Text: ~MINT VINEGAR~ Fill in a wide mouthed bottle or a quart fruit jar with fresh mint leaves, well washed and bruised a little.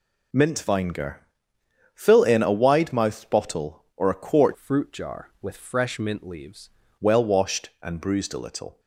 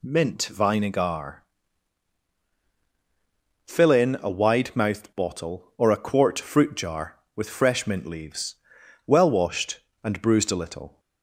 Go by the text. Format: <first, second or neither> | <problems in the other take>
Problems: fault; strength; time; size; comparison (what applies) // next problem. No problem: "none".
second | changes voice from "fruit" to "leaves"; from 4.5 to 6.6 s; 2.1 s long